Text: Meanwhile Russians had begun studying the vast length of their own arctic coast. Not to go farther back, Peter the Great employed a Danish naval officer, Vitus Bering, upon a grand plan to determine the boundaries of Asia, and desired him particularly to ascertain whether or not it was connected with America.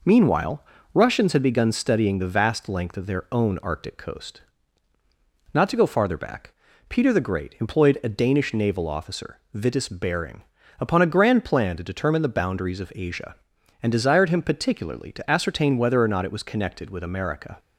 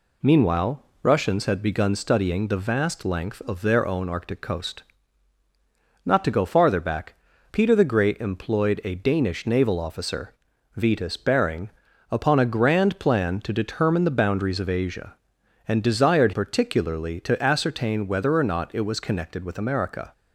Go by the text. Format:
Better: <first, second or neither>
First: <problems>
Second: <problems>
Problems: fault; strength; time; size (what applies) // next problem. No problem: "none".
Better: first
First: pauses between "Meanwhile" and "Russians"; slight; at 0.6 s; 0.30 s long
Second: pauses between "Meanwhile" and "Russians"; slight; at 0.8 s; 0.22 s long // skips "him"; at 16.3 s